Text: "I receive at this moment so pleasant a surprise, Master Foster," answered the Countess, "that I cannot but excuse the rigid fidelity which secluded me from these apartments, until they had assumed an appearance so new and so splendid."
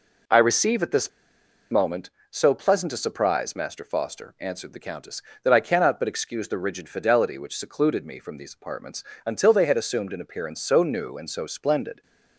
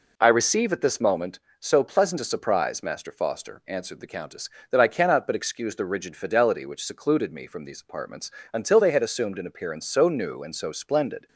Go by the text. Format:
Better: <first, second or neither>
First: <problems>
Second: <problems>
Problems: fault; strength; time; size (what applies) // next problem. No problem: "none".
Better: second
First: pauses between "this" and "moment"; noticeable; at 1.0 s; 0.62 s long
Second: none